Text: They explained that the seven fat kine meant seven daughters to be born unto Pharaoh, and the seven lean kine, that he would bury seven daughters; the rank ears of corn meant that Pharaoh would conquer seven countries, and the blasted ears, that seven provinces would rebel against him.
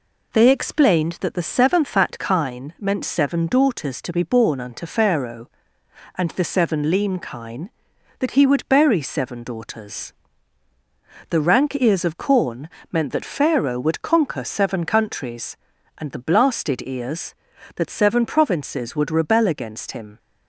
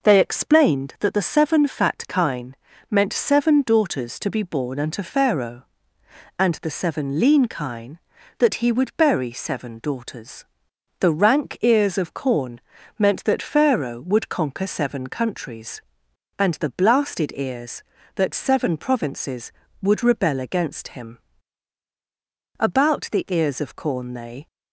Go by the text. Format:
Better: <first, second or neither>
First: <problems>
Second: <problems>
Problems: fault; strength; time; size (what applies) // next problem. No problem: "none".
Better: first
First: pauses between "corn" and "meant"; slight; at 12.6 s; 0.22 s long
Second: pauses between "kine" and "meant"; slight; at 2.5 s; 0.34 s long // pauses between "corn" and "meant"; slight; at 12.6 s; 0.36 s long // goes on to say "About the ears of corn they"; strong; from 22.5 s on; 1.9 s long